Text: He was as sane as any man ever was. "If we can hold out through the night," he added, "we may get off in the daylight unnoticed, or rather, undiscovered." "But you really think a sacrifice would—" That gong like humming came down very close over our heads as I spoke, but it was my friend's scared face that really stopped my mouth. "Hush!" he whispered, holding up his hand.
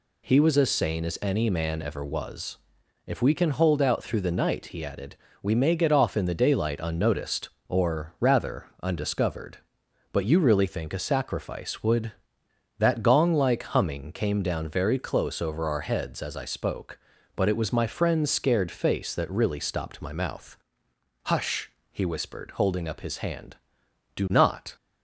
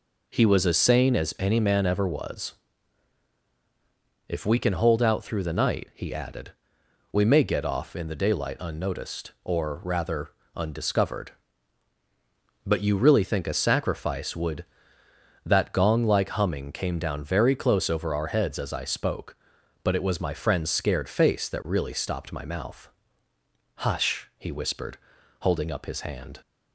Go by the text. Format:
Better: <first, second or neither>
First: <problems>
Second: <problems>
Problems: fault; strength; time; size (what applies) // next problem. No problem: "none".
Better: second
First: goes on to say "Do not"; from 24.1 s on; 0.60 s long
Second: none